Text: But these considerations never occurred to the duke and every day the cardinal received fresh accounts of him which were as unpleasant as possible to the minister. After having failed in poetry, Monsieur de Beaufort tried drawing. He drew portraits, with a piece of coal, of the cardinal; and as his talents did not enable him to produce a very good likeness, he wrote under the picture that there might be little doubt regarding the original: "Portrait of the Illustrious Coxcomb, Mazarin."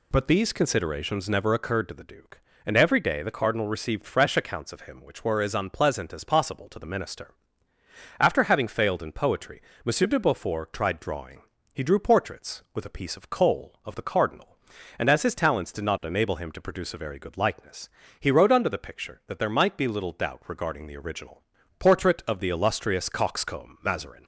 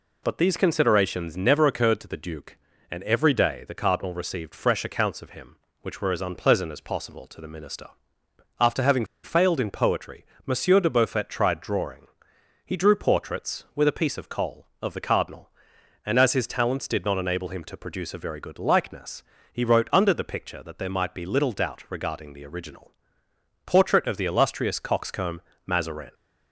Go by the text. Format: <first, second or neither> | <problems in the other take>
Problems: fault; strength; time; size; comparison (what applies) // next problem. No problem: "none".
first | pauses between "having" and "failed"; slight; at 9.0 s; 0.19 s long